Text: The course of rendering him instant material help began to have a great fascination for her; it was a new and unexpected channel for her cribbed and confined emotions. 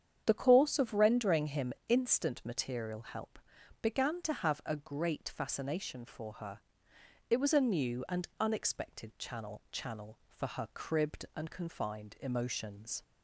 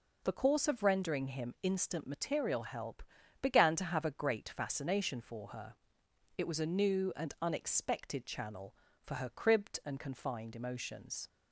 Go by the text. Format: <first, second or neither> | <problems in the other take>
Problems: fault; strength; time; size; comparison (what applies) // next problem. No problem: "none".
second | starts louder than the rest; strong; until 1.2 s; 8 dB // pauses between "him" and "instant"; slight; at 1.7 s; 0.16 s long // pauses between "help" and "began"; at 3.3 s; 0.42 s long; also in the second // says "channel" twice; at 9.7 s